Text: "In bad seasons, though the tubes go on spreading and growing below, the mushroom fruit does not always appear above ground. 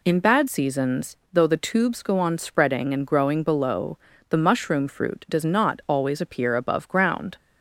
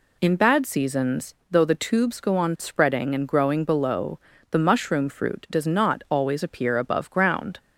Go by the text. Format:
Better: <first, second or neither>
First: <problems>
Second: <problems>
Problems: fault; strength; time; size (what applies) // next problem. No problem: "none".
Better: neither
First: none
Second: none